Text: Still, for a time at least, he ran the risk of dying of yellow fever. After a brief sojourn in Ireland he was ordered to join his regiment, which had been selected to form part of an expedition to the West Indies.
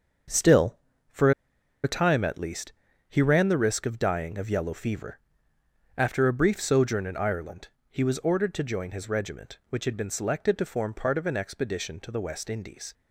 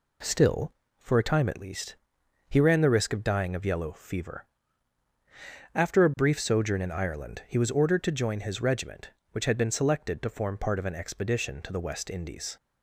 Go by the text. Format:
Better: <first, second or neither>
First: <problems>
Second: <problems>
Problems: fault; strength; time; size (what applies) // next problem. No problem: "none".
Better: second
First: starts louder than the rest; until 2.1 s; 7 dB // pauses between "for" and "a"; noticeable; at 1.3 s; 0.52 s long // pauses between "Ireland" and "he"; slight; at 7.6 s; 0.24 s long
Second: none